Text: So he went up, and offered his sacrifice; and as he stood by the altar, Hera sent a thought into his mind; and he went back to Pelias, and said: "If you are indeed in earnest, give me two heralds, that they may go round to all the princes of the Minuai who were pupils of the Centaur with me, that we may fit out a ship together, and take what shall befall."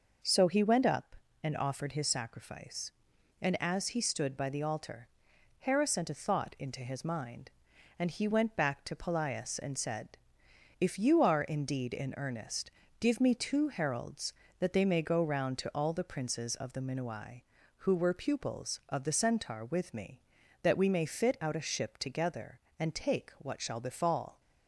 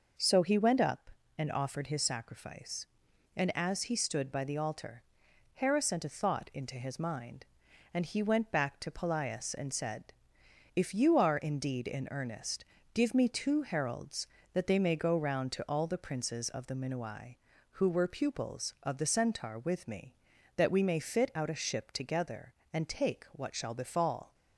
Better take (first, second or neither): neither